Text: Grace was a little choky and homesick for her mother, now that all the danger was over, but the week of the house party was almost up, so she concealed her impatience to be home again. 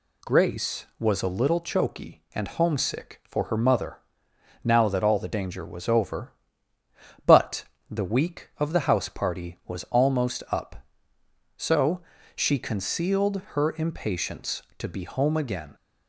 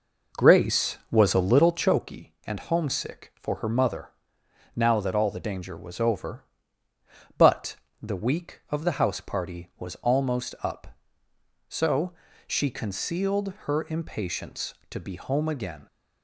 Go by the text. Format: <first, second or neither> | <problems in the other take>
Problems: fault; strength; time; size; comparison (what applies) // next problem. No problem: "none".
first | starts louder than the rest; noticeable; until 2.1 s; 4.5 dB // pauses between "but" and "the"; slight; at 7.7 s; 0.24 s long; slight in the first // pauses between "so" and "she"; slight; at 12.1 s; 0.34 s long; slight in the first